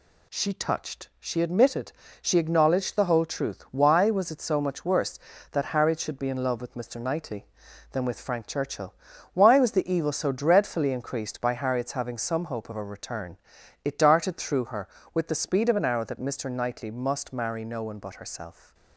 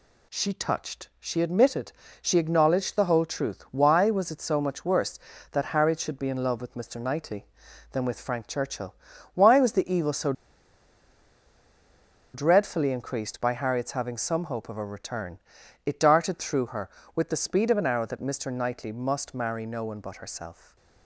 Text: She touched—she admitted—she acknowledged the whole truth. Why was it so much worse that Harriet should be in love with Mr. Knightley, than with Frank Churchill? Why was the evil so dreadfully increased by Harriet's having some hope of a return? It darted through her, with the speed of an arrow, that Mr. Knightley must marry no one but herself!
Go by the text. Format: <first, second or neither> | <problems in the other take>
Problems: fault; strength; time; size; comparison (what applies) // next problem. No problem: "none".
first | pauses between "so" and "dreadfully"; strong; at 10.3 s; 2.0 s long // stays silent after the last word; slight; from 20.5 s on; 0.5 s long